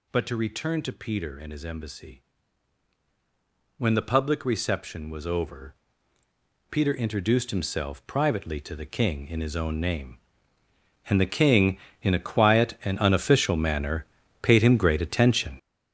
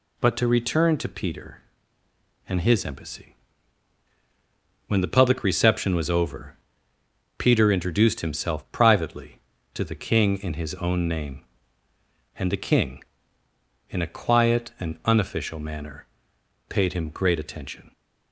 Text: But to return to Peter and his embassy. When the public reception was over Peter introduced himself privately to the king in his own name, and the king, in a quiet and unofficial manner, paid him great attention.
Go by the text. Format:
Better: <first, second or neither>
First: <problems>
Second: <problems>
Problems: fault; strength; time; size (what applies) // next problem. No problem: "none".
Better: second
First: gets louder; strong; throughout; 10.5 dB // pauses between "over" and "Peter"; noticeable; at 5.7 s; 0.96 s long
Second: pauses between "over" and "Peter"; noticeable; at 6.5 s; 0.84 s long